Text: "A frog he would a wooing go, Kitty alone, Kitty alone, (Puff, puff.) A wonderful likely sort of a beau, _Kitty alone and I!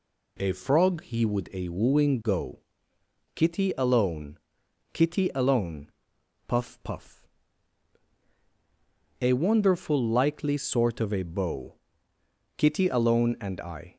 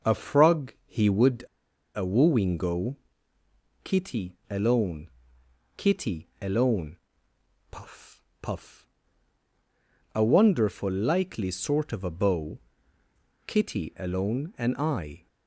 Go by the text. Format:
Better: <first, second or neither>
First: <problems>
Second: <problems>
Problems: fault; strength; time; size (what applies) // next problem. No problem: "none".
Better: first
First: none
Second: pauses between "would" and "a"; noticeable; at 1.4 s; 0.51 s long